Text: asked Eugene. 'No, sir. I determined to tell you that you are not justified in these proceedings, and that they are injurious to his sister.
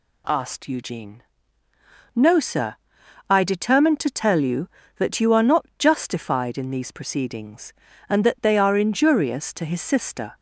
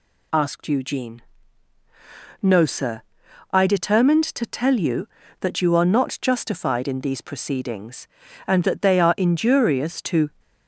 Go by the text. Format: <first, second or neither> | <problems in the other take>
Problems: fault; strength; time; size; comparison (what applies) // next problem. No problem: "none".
first | stops before "his sister"; at 10.3 s